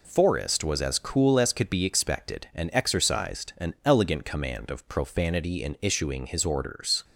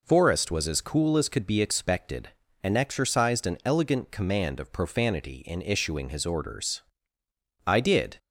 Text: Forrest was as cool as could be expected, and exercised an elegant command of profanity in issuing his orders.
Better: first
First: none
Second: goes on to say "I did"; from 7.6 s on; 0.52 s long

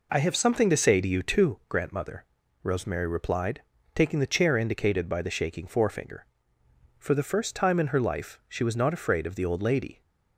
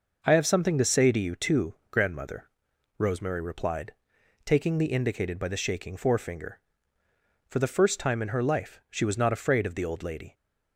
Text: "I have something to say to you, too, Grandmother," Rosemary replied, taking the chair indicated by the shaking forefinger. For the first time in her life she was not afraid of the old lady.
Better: first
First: none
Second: skips "chair"; at 4.9 s

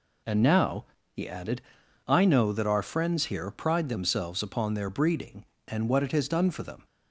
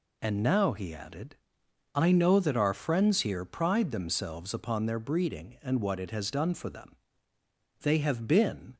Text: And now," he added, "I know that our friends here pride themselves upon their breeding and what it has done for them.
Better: first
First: none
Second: goes on to say "They have been"; noticeable; from 7.8 s on; 0.96 s long

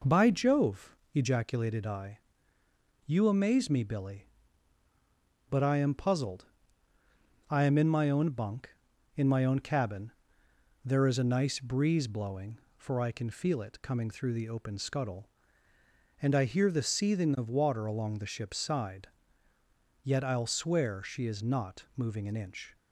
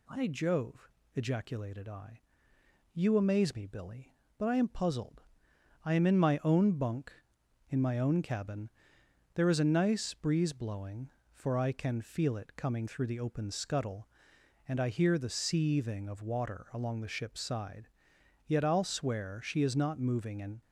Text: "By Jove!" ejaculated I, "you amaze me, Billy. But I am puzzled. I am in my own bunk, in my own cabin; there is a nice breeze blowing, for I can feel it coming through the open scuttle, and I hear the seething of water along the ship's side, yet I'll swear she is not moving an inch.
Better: first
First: none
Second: stops before "inch"; at 20.6 s

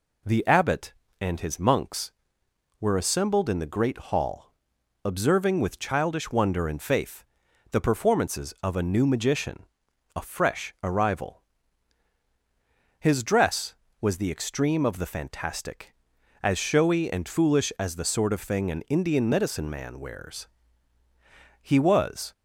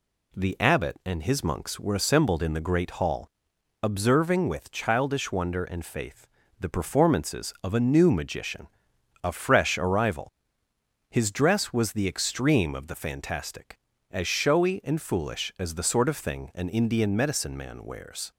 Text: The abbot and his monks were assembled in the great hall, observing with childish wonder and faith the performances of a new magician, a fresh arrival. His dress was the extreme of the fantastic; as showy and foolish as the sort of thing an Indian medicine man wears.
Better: second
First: pauses between "faith" and "the"; noticeable; at 7.2 s; 0.48 s long // goes on to say "He was"; noticeable; from 21.6 s on; 0.72 s long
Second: pauses between "faith" and "the"; slight; at 6.2 s; 0.30 s long

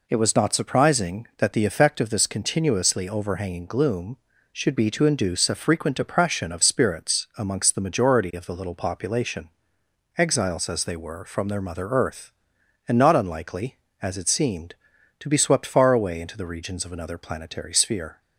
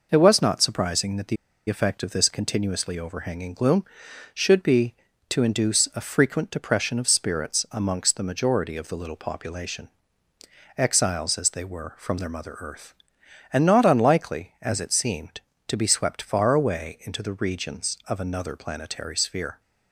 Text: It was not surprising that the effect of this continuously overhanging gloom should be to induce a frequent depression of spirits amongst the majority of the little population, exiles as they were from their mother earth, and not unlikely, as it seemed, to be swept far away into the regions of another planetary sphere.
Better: first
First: none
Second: pauses between "the" and "effect"; slight; at 1.3 s; 0.32 s long

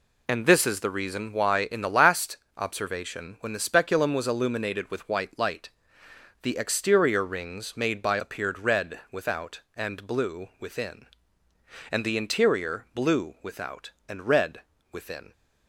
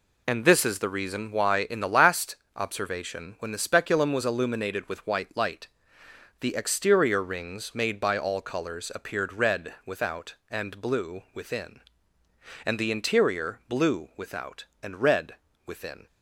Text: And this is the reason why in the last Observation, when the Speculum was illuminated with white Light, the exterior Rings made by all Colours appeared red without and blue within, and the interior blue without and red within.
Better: second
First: pauses between "last" and "Observation"; slight; at 2.3 s; 0.20 s long // skips "all Colours"; at 8.1 s // pauses between "red" and "within"; slight; at 14.5 s; 0.32 s long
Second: pauses between "last" and "Observation"; slight; at 2.3 s; 0.20 s long // pauses between "red" and "within"; slight; at 15.3 s; 0.32 s long

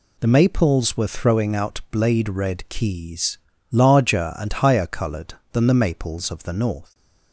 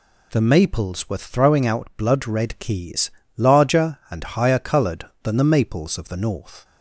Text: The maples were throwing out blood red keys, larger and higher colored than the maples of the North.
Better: second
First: says "blade" for "blood"; at 1.9 s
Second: none

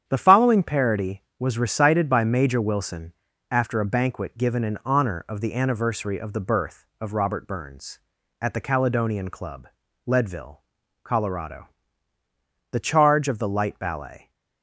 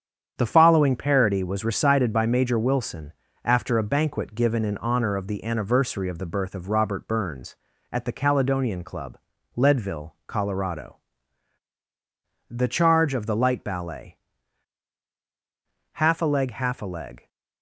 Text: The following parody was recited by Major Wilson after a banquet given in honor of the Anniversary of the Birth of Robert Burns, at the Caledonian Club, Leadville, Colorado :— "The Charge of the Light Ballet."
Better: first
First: starts louder than the rest; strong; until 1.0 s; 9 dB // pauses between "Wilson" and "after"; at 3.1 s; 0.38 s long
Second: starts louder than the rest; strong; until 1.3 s; 8 dB // pauses between "Wilson" and "after"; slight; at 3.1 s; 0.28 s long // goes on to say "Half a leg half a leg"; from 15.9 s on; 1.3 s long

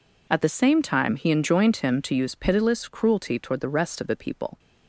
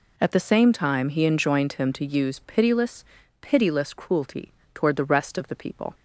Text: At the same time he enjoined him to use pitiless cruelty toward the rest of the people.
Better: first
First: none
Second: says "pitiless" twice; at 3.4 s // pauses between "cruelty" and "toward"; slight; at 4.5 s; 0.20 s long

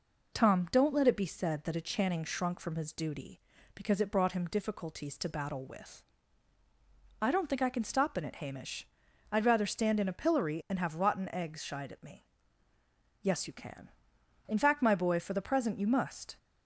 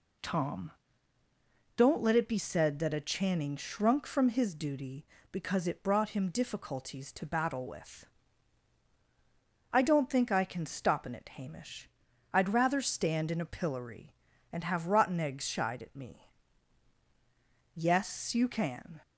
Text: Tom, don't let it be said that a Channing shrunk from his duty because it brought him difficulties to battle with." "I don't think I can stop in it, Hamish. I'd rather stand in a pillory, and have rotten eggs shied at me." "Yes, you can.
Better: second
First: goes on to say "In fact my boy for the present you must"; strong; from 14.4 s on; 1.9 s long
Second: none

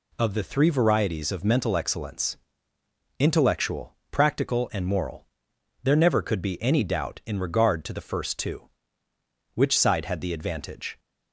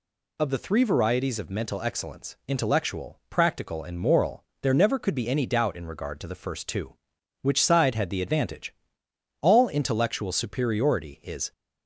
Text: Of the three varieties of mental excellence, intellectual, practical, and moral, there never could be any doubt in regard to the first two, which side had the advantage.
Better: first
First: none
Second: goes on to say "All intellectual superiority is"; strong; from 9.4 s on; 2.1 s long

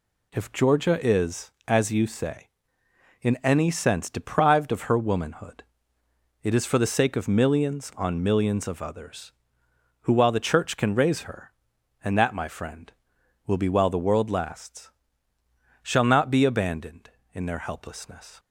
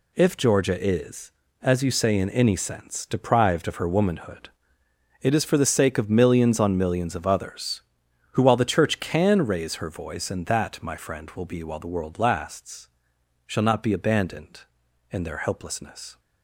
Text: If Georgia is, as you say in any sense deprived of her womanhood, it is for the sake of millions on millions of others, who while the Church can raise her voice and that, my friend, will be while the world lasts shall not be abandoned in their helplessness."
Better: second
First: skips "voice"; at 11.7 s // pauses between "lasts" and "shall"; noticeable; at 14.8 s; 0.94 s long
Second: pauses between "lasts" and "shall"; noticeable; at 12.8 s; 0.58 s long

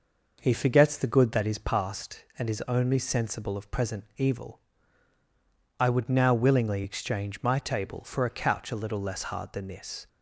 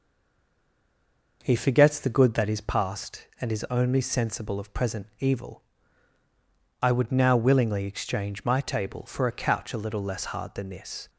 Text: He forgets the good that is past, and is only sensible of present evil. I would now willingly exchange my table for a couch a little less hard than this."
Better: first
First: none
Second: stays silent before the first word; noticeable; until 1.4 s; 1.4 s long

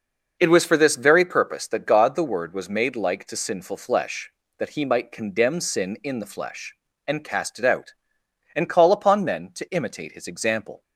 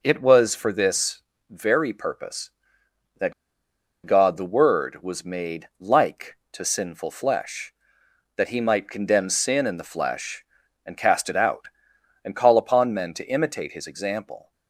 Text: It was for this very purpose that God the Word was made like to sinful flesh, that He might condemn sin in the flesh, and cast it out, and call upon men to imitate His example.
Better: first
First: none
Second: pauses between "this" and "very"; slight; at 1.2 s; 0.28 s long // pauses between "that" and "God"; noticeable; at 3.3 s; 0.72 s long

